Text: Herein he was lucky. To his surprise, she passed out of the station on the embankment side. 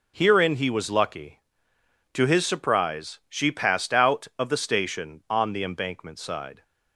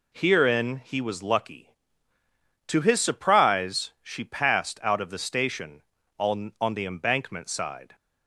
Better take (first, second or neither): first